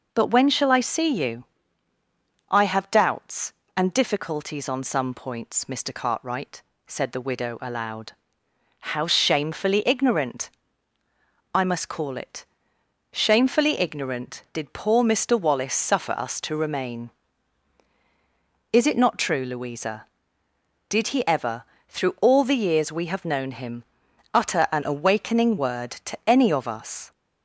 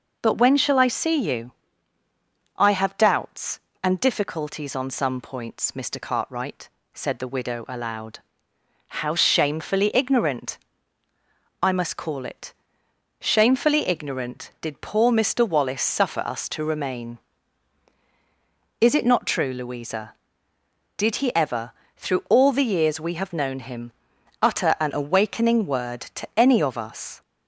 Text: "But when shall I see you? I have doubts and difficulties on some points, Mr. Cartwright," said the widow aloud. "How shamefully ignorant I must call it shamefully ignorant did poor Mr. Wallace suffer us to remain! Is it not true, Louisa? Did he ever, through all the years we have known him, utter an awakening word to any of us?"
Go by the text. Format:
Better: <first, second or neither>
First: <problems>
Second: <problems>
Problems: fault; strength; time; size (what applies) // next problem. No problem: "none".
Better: neither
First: pauses between "ignorant" and "I"; at 10.4 s; 1.0 s long // pauses between "it" and "shamefully"; noticeable; at 12.4 s; 0.68 s long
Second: pauses between "ignorant" and "I"; at 10.5 s; 1.0 s long // pauses between "it" and "shamefully"; noticeable; at 12.5 s; 0.68 s long